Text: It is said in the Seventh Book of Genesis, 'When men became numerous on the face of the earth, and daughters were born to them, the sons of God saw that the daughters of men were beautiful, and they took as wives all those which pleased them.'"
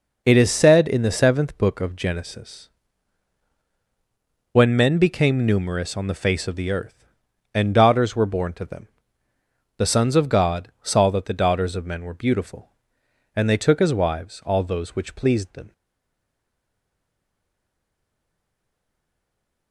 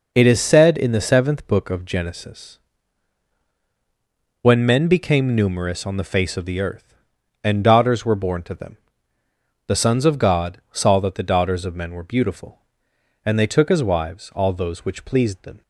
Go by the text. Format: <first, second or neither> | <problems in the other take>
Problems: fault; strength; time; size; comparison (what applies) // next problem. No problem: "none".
second | stays silent after the last word; strong; from 15.7 s on; 4.0 s long